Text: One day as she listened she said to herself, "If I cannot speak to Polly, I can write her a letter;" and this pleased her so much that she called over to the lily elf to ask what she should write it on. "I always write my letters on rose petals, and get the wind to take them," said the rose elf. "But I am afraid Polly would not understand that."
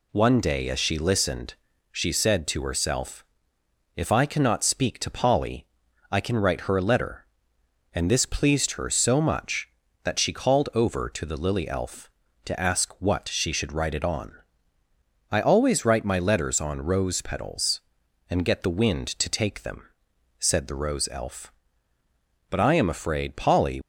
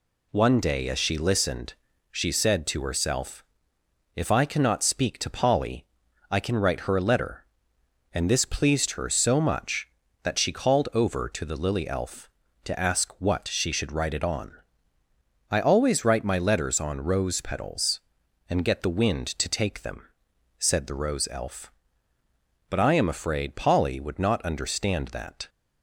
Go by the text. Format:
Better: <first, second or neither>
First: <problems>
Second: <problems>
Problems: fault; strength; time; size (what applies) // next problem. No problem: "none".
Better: second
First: pauses between "listened" and "she"; at 1.5 s; 0.38 s long // stops before "would not understand that"; at 23.8 s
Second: pauses between "listened" and "she"; at 1.7 s; 0.38 s long